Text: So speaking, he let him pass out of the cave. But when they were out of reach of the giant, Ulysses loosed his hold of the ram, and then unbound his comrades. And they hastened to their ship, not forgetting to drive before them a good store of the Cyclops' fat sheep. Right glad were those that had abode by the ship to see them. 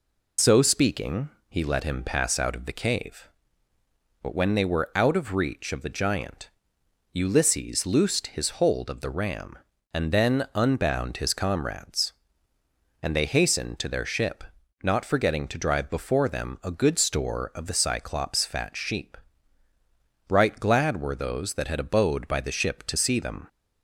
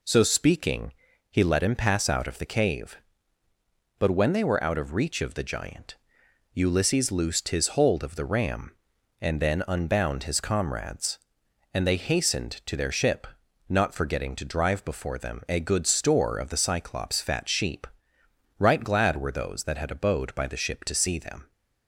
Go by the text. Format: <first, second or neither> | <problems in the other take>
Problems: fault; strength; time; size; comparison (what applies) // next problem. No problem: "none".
second | loses the start of "So"; at 0.3 s; 85 ms